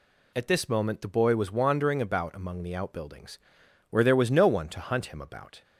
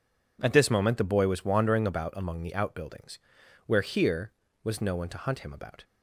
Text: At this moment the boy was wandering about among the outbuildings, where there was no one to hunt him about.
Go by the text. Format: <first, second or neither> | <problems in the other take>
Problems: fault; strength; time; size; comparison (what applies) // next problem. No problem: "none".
first | says "here" for "there"; at 3.8 s